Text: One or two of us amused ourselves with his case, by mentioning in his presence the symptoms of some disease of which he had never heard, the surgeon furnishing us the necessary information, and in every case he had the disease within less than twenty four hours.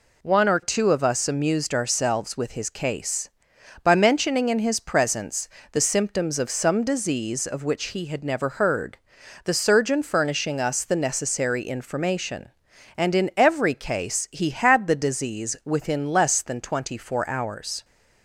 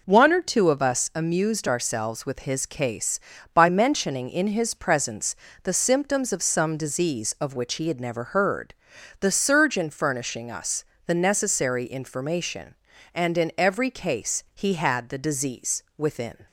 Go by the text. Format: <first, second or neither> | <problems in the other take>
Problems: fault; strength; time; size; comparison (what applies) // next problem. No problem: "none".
first | pauses between "presence" and "the"; slight; at 5.3 s; 0.26 s long; slight in the first // pauses between "us" and "the"; slight; at 10.8 s; 0.22 s long // stops before "less than twenty four hours"; at 16.4 s